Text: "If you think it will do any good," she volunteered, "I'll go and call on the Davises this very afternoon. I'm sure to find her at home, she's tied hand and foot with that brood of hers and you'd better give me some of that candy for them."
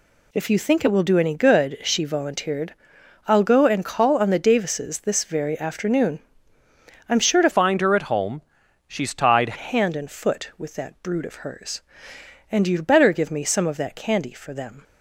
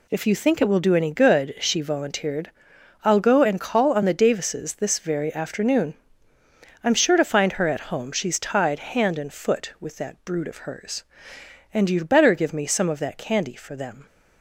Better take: second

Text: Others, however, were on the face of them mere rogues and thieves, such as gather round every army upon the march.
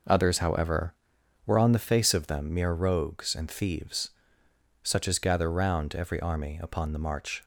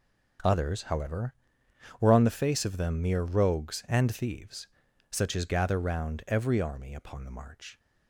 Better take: neither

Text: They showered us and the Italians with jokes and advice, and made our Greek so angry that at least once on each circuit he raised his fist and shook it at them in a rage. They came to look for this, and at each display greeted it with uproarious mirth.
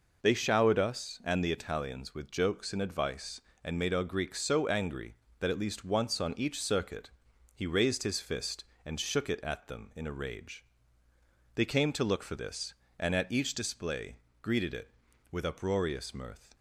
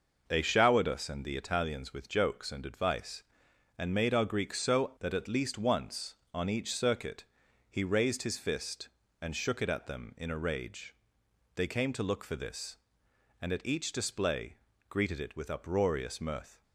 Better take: first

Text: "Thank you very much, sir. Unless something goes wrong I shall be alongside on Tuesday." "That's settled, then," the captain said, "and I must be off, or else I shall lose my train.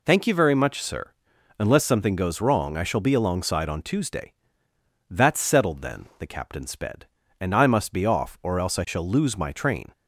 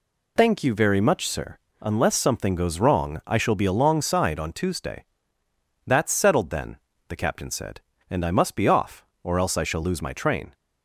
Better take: second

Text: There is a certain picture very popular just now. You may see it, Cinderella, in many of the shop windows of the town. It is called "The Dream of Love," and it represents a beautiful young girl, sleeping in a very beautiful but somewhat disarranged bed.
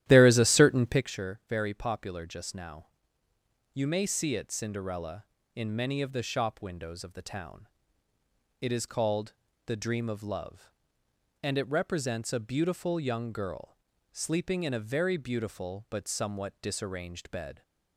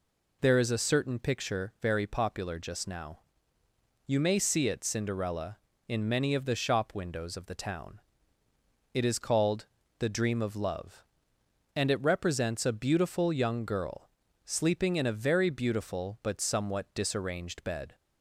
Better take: second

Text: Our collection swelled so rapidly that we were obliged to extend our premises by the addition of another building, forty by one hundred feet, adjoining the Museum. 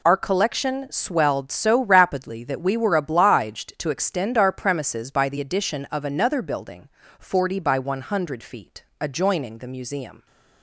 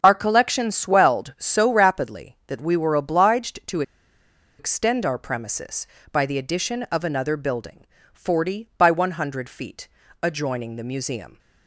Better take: first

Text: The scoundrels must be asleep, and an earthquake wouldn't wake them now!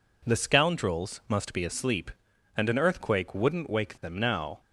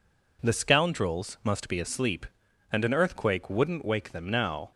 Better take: neither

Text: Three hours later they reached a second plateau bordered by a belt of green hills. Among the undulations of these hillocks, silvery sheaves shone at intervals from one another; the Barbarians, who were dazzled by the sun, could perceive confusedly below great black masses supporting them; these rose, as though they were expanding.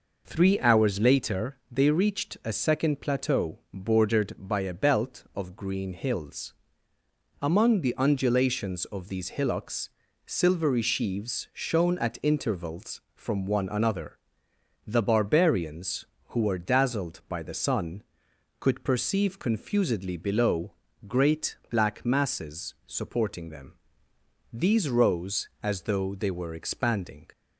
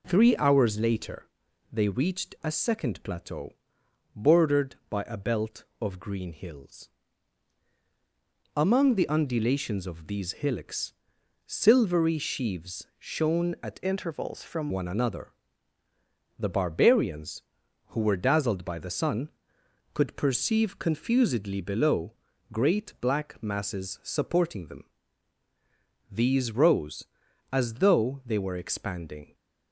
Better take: first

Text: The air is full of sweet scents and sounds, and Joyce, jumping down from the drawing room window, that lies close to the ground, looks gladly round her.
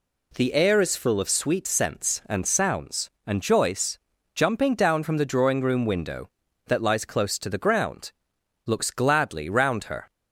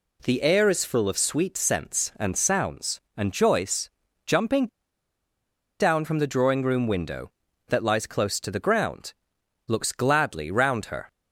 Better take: first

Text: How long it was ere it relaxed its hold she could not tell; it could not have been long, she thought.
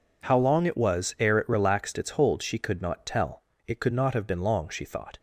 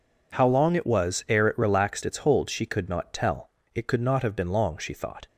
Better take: neither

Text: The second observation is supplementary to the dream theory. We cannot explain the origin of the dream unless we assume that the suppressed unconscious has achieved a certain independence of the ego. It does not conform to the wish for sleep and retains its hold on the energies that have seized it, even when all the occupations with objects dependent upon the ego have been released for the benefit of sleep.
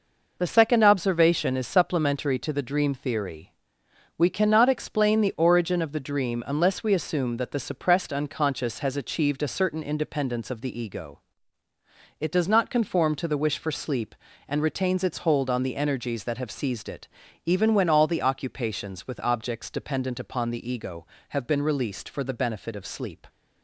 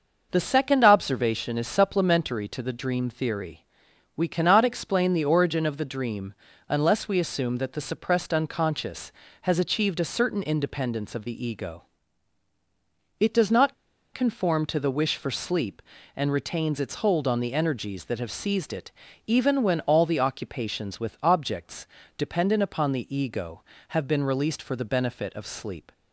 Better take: first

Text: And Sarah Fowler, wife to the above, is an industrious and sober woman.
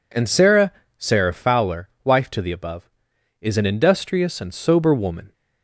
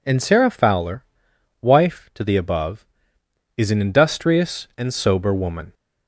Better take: second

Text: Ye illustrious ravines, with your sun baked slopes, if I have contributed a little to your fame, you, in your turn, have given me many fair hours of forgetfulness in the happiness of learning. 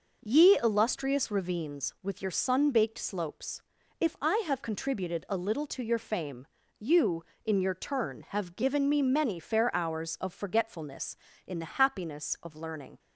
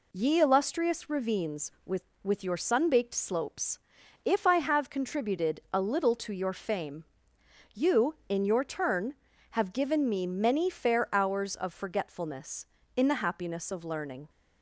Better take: first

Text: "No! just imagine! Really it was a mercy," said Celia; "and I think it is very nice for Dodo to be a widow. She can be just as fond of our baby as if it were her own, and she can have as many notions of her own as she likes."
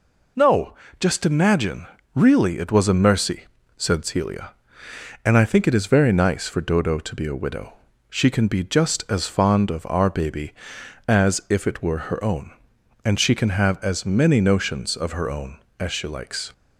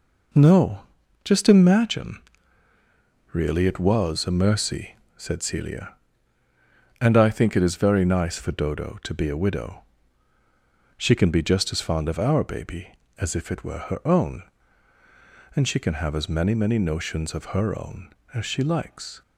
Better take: first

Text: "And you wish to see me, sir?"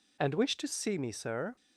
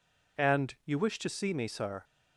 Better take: second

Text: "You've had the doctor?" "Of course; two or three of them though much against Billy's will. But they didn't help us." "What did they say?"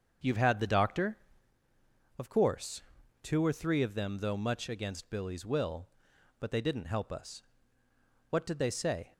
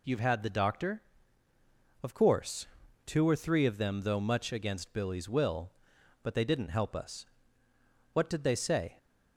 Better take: second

